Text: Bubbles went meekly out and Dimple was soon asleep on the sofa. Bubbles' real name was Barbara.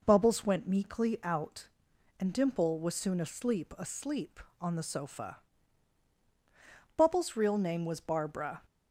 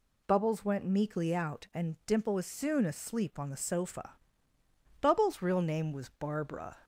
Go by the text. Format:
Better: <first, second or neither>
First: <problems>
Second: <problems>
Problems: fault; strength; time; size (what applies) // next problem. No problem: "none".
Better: second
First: says "asleep" twice; at 3.7 s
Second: none